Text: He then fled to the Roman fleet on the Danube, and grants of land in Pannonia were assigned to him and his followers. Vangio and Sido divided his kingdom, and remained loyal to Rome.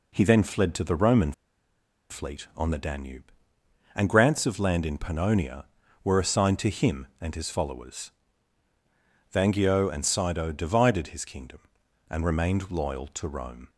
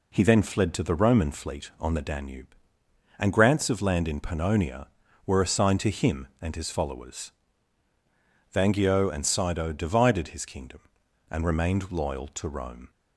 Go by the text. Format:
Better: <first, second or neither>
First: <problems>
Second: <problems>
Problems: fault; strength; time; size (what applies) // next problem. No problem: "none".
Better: second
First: pauses between "Roman" and "fleet"; noticeable; at 1.3 s; 0.78 s long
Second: none